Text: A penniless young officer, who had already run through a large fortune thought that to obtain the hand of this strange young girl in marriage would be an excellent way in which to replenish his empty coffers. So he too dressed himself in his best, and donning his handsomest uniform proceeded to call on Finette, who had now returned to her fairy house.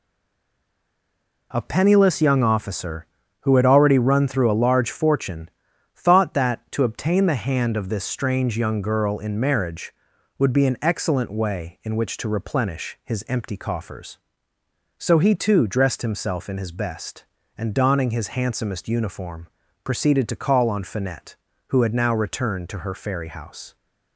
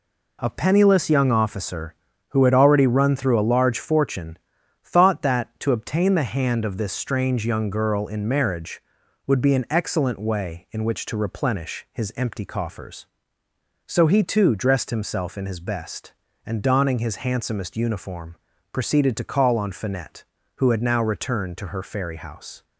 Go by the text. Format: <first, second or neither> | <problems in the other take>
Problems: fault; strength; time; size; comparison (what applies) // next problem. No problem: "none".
second | stays silent before the first word; noticeable; until 1.5 s; 1.5 s long // pauses between "fortune" and "thought"; at 5.4 s; 0.44 s long; also in the second // pauses between "uniform" and "proceeded"; slight; at 19.4 s; 0.36 s long; slight in the second